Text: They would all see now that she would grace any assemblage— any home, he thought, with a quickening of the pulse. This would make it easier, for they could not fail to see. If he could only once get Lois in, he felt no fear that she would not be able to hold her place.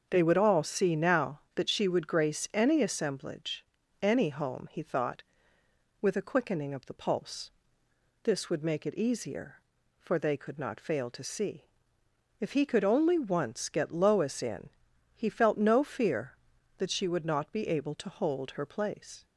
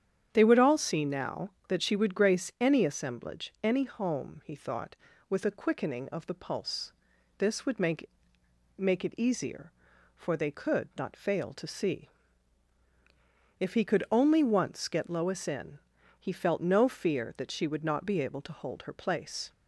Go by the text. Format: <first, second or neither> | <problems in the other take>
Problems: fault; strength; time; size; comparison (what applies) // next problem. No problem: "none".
first | starts louder than the rest; strong; until 1.3 s; 9 dB; also in the first // says "make" twice; at 8.7 s